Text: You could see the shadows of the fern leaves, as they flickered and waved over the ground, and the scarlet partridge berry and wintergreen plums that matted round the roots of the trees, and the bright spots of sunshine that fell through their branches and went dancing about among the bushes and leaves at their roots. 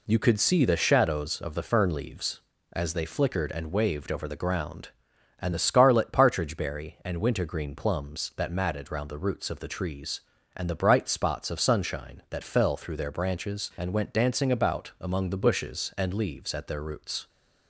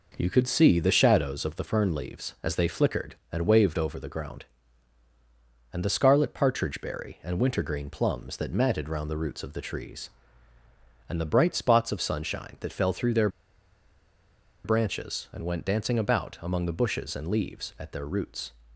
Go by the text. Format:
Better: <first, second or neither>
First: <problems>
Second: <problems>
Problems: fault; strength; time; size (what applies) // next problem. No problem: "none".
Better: first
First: none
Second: pauses between "their" and "branches"; strong; at 13.2 s; 1.3 s long